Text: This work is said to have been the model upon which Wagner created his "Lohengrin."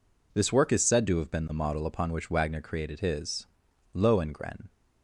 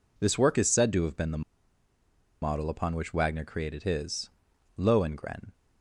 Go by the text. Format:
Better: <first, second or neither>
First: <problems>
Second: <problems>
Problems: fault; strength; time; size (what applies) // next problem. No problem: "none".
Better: first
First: pauses between "his" and "Lohengrin"; noticeable; at 3.4 s; 0.46 s long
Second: pauses between "the" and "model"; at 1.4 s; 1.0 s long // pauses between "his" and "Lohengrin"; noticeable; at 4.3 s; 0.46 s long